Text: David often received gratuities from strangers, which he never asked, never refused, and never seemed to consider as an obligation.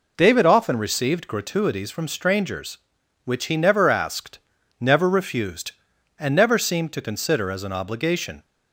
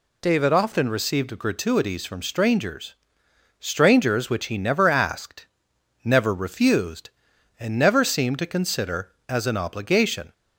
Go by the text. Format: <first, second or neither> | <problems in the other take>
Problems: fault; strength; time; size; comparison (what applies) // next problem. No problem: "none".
first | says "strangers" twice; at 3.6 s